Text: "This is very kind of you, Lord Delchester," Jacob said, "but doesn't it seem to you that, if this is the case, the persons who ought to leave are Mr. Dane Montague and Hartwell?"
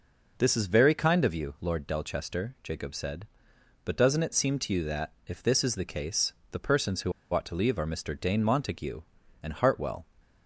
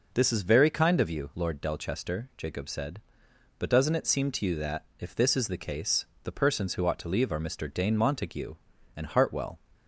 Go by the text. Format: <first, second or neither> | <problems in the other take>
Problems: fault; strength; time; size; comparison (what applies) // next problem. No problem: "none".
second | pauses between "who" and "ought"; slight; at 7.1 s; 0.20 s long